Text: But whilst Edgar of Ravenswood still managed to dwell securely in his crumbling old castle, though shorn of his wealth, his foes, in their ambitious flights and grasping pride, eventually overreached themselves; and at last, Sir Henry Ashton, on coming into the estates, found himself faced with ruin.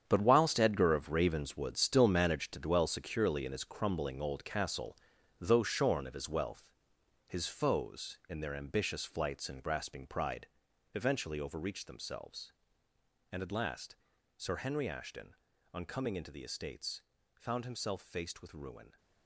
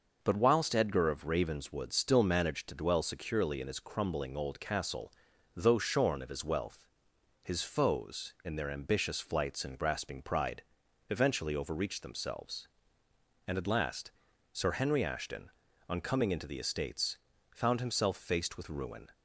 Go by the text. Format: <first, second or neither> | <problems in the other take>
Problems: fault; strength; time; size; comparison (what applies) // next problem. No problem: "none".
second | gets quieter; strong; throughout; 12 dB